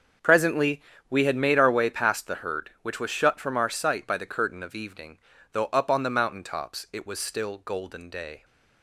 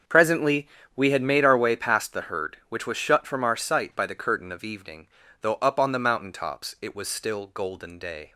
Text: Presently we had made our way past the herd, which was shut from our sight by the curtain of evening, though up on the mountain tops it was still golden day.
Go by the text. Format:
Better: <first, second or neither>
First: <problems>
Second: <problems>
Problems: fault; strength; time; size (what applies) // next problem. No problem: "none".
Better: neither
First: starts louder than the rest; until 1.5 s; 7 dB // pauses between "Presently" and "we"; slight; at 0.8 s; 0.28 s long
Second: starts louder than the rest; until 1.3 s; 6.5 dB // pauses between "Presently" and "we"; slight; at 0.6 s; 0.28 s long